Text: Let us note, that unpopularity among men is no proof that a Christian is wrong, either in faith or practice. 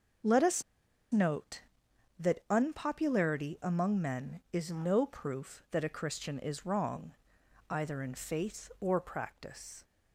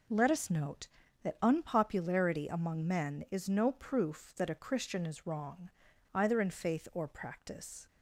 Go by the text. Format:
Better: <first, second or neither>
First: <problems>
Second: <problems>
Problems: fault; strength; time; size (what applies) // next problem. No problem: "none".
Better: second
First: starts louder than the rest; until 2.3 s; 6.5 dB // pauses between "us" and "note"; noticeable; at 0.6 s; 0.51 s long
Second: none